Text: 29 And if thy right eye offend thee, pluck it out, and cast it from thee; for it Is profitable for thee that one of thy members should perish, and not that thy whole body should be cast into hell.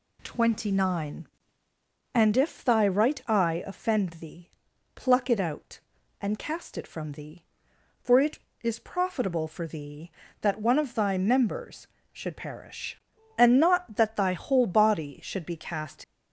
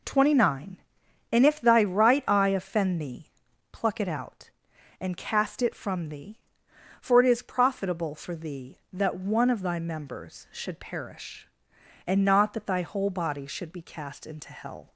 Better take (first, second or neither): second